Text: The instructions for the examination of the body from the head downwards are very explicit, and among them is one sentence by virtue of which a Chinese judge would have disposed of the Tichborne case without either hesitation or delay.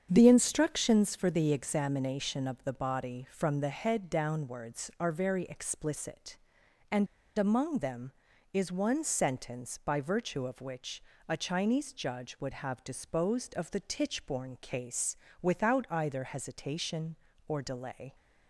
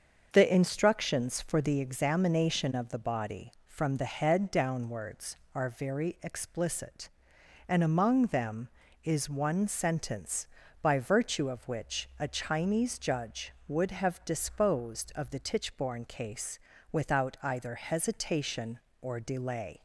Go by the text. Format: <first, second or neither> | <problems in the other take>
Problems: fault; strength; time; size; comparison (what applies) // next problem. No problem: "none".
second | starts louder than the rest; strong; until 1.1 s; 8 dB; also in the second // pauses between "and" and "among"; slight; at 7.0 s; 0.30 s long // pauses between "which" and "a"; slight; at 11.0 s; 0.24 s long // pauses between "case" and "without"; slight; at 15.1 s; 0.24 s long; slight in the second